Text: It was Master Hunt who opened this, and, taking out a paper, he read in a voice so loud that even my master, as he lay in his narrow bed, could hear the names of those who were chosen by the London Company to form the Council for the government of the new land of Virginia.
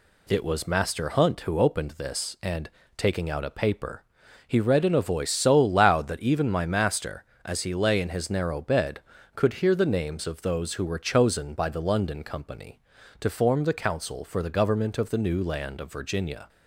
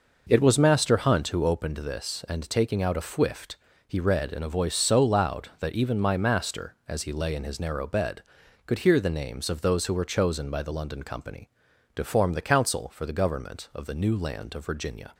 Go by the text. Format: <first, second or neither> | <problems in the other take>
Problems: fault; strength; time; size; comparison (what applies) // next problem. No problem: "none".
first | says "fwift" for "paper"; at 3.0 s